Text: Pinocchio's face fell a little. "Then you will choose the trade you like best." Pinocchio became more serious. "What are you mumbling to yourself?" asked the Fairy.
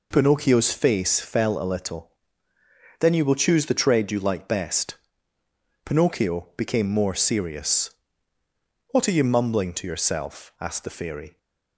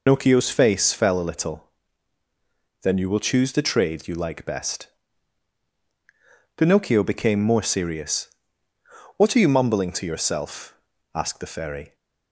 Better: first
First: none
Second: loses the start of "Pinocchio's"; at 0.0 s; 120 ms

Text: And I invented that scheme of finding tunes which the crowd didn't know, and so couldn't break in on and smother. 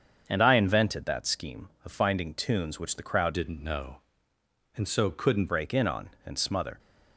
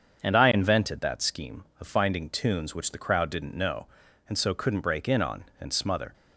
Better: second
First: starts louder than the rest; strong; until 1.2 s; 7 dB // changes voice from "didn't" to "couldn't"; from 3.3 to 5.5 s; 2.2 s long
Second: starts louder than the rest; until 1.2 s; 7 dB

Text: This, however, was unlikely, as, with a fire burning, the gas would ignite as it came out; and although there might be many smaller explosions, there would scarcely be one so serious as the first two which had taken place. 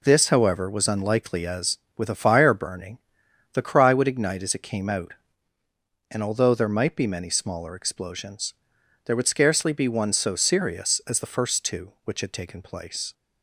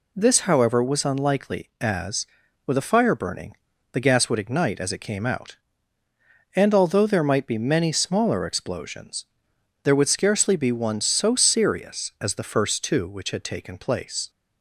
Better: second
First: says "cry" for "gas"; at 3.6 s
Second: none

